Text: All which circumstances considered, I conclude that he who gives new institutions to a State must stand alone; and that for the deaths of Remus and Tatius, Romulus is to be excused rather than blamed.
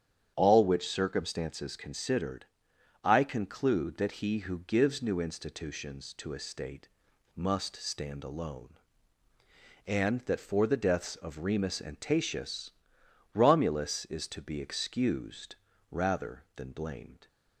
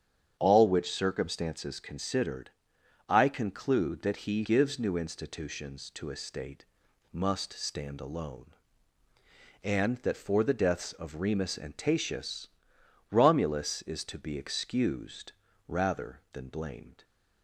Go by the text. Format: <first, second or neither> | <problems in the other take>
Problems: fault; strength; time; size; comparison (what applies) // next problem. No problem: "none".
first | starts louder than the rest; strong; until 1.4 s; 8.5 dB; strong in the first // skips "who"; at 4.4 s // pauses between "State" and "must"; noticeable; at 6.6 s; 0.46 s long; noticeable in the first // pauses between "excused" and "rather"; slight; at 15.3 s; 0.36 s long; slight in the first